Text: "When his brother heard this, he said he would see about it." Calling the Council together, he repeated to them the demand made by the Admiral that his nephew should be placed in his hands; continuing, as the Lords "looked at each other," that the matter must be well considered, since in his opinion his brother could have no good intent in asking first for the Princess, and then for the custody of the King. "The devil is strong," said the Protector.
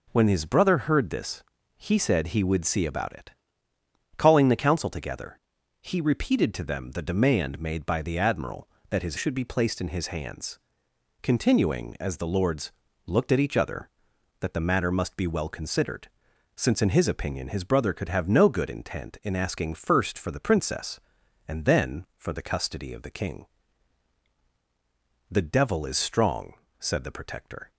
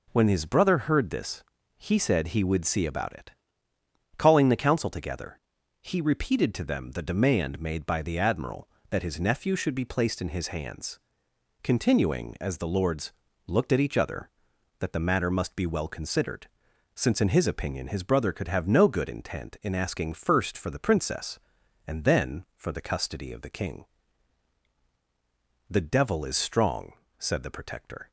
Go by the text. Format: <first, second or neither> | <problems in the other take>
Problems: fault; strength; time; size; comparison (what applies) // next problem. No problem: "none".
second | skips "nephew"; at 9.1 s // pauses between "Lords" and "looked"; slight; at 12.7 s; 0.32 s long; slight in the second